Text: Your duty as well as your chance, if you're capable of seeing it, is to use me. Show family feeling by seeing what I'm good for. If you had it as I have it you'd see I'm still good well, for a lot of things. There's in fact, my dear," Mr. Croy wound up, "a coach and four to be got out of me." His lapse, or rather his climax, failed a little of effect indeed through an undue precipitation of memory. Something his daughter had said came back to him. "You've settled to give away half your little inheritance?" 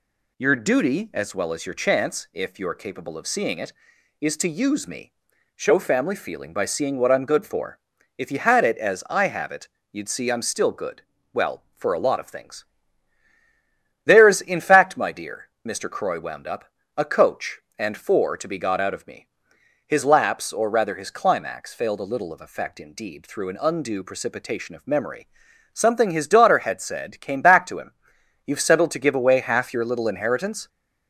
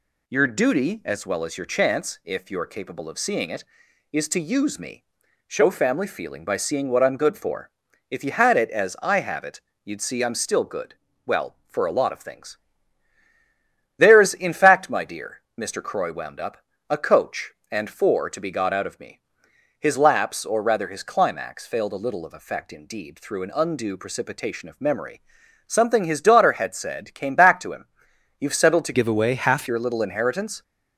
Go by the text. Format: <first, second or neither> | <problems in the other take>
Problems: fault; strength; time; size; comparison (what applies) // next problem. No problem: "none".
first | pauses between "it" and "you'd"; slight; at 9.5 s; 0.24 s long; slight in the first // pauses between "good" and "well"; slight; at 10.9 s; 0.32 s long; slight in the first // changes voice from "give" to "half"; from 28.9 to 29.6 s; 0.7 s long